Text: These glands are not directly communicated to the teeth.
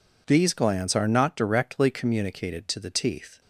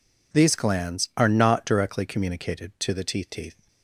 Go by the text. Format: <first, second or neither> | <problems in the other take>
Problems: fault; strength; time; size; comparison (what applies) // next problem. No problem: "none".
first | says "teeth" twice; at 3.2 s